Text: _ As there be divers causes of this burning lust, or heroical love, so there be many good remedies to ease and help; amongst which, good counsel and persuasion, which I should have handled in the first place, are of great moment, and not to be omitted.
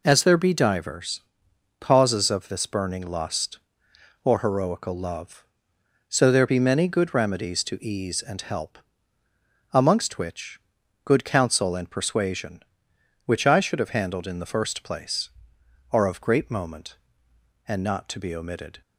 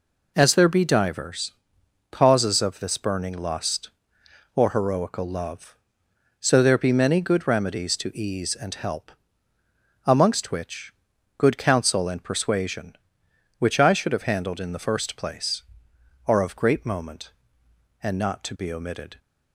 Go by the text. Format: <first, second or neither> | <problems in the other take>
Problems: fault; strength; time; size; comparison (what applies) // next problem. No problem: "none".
neither | pauses between "divers" and "causes"; noticeable; the same in both